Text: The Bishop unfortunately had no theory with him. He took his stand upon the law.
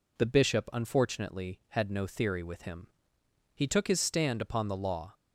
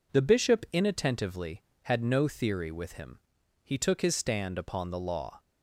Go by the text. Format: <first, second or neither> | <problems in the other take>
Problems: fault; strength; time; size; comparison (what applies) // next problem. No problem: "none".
first | says "inattentively" for "unfortunately"; at 0.7 s